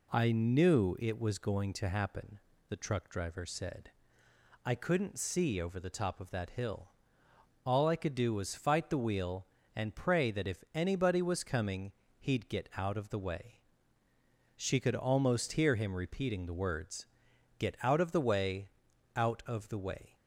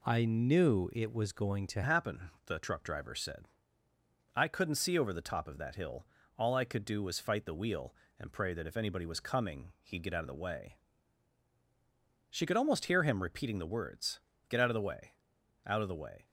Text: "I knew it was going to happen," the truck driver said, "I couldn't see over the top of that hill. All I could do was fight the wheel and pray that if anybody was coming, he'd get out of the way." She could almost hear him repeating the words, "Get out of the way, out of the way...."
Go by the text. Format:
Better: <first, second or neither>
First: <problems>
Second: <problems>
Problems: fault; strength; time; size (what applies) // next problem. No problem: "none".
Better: first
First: none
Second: changes voice at "happen"; from 1.8 s on; 14.4 s long